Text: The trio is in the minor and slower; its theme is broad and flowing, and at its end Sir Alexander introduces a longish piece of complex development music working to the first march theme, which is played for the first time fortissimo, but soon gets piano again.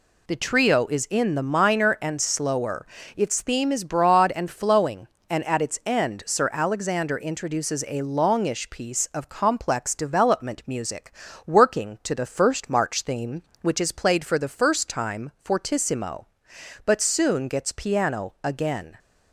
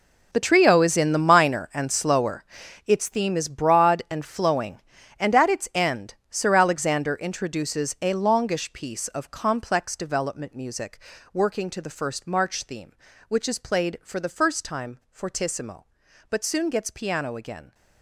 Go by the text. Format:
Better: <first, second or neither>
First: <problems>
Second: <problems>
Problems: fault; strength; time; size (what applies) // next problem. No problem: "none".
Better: first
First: pauses between "music" and "working"; slight; at 11.1 s; 0.34 s long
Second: gets quieter; strong; throughout; 14.5 dB // pauses between "end" and "Sir"; slight; at 6.1 s; 0.16 s long // pauses between "music" and "working"; slight; at 10.9 s; 0.34 s long